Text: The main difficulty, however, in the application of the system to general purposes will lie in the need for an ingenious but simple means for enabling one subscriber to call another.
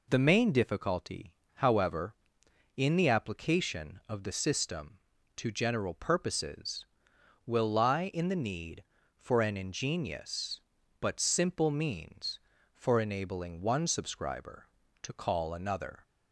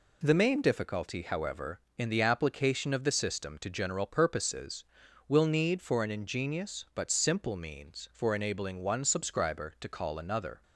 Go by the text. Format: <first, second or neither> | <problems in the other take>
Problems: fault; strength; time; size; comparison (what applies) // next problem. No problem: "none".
first | skips "lie in the"; at 5.4 s